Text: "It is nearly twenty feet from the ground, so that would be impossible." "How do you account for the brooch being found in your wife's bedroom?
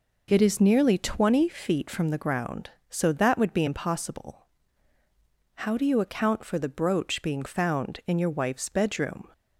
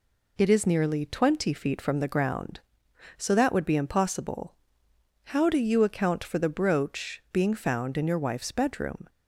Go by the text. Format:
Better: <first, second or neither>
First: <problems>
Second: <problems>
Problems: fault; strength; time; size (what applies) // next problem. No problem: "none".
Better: neither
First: none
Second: none